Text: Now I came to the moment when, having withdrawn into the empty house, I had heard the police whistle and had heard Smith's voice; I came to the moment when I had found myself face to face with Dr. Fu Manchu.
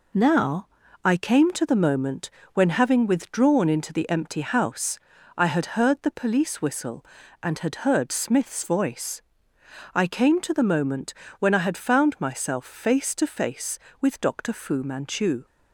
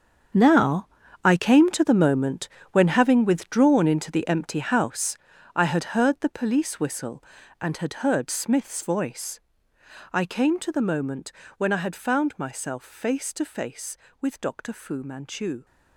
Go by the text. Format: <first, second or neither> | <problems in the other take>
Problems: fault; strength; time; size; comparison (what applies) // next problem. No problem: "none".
first | gets quieter; strong; throughout; 14 dB // pauses between "Now" and "I"; slight; at 0.8 s; 0.36 s long; slight in the first // pauses between "moment" and "when"; slight; at 2.4 s; 0.24 s long; slight in the first // pauses between "moment" and "when"; slight; at 11.3 s; 0.24 s long; slight in the first